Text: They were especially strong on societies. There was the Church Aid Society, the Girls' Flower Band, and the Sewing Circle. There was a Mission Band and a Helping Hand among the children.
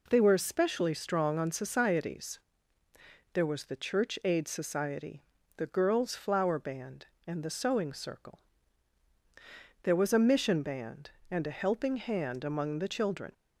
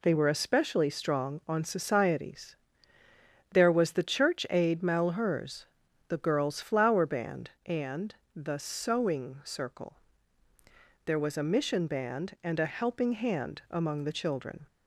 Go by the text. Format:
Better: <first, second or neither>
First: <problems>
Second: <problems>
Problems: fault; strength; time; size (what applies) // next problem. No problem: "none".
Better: first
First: none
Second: says "Malheurs" for "Society"; at 4.8 s // pauses between "and" and "the"; slight; at 8.1 s; 0.20 s long